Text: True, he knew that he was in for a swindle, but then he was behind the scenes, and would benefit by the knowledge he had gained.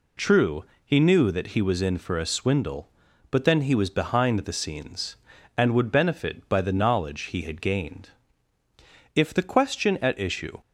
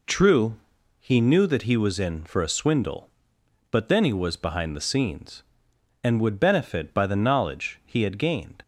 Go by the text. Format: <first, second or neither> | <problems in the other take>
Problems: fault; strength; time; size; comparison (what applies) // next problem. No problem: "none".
second | goes on to say "If the question at issue"; from 9.1 s on; 1.4 s long